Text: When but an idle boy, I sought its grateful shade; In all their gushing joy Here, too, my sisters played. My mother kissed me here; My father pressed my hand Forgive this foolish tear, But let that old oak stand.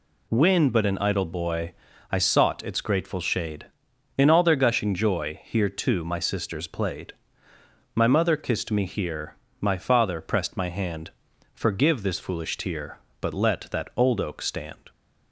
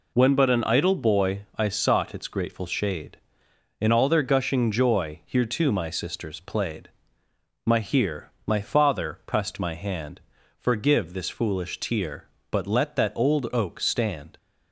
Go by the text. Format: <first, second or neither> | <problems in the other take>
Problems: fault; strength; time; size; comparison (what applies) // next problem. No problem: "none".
first | skips "mother kissed me"; at 7.7 s // pauses between "hand" and "Forgive"; at 10.2 s; 0.38 s long; noticeable in the first